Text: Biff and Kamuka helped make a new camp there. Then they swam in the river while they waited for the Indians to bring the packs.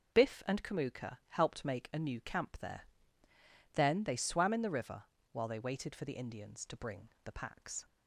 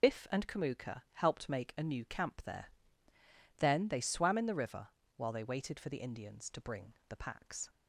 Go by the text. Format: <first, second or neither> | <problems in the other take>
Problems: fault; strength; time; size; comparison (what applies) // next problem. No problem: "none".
first | loses the start of "Biff"; at 0.0 s; 40 ms // pauses between "river" and "while"; slight; at 4.8 s; 0.30 s long; slight in the first // pauses between "bring" and "the"; slight; at 6.9 s; 0.16 s long; slight in the first